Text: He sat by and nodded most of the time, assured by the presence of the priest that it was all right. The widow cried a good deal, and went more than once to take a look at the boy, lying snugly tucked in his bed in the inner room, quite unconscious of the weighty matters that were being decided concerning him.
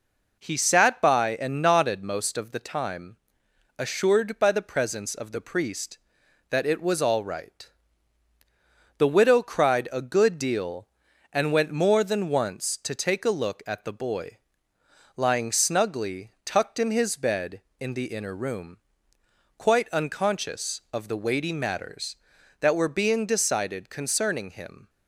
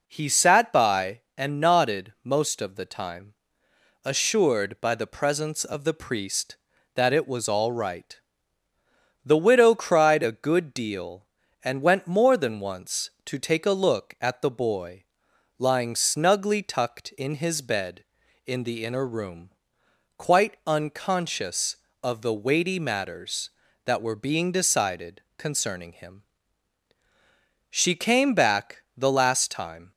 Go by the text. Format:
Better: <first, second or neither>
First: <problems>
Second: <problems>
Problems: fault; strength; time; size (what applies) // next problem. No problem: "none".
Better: first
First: none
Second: pauses between "decided" and "concerning"; slight; at 25.2 s; 0.16 s long // goes on to say "She came back the last time"; strong; from 27.7 s on; 2.2 s long